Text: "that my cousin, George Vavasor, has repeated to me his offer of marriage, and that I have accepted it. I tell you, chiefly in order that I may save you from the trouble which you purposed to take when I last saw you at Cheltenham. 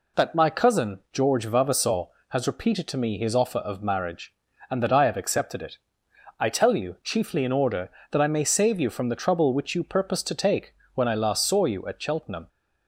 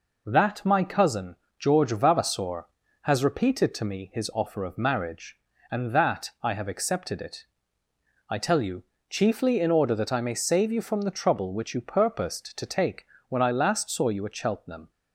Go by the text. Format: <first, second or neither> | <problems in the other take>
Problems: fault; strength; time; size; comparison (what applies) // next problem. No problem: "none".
neither | pauses between "take" and "when"; slight; the same in both